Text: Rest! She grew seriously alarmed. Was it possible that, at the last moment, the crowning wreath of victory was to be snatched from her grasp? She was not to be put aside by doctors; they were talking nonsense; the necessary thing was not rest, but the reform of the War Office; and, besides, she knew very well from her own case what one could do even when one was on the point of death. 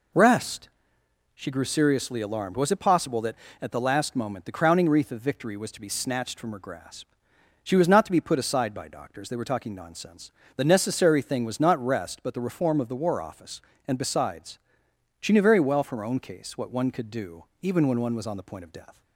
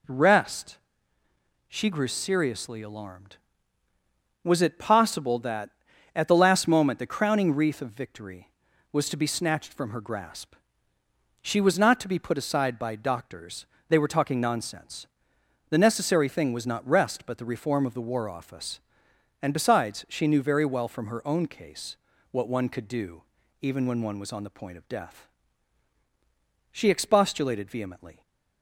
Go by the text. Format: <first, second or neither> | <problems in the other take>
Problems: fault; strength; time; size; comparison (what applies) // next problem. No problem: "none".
first | pauses between "case" and "what"; slight; at 21.9 s; 0.32 s long // pauses between "do" and "even"; slight; at 23.2 s; 0.36 s long; slight in the first // goes on to say "She expostulated vehemently"; from 26.7 s on; 1.5 s long